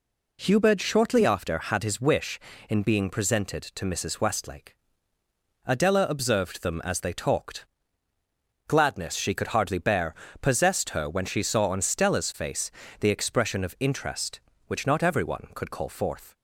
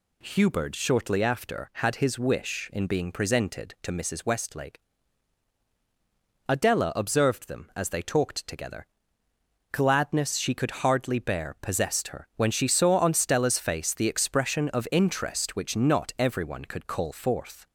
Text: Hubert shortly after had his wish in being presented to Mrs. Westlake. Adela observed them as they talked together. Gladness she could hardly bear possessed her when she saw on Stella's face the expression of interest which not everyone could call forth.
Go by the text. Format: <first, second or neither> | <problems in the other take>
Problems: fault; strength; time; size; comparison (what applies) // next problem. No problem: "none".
second | skips "together"; at 8.1 s // pauses between "bear" and "possessed"; slight; at 10.1 s; 0.26 s long // pauses between "face" and "the"; slight; at 12.7 s; 0.30 s long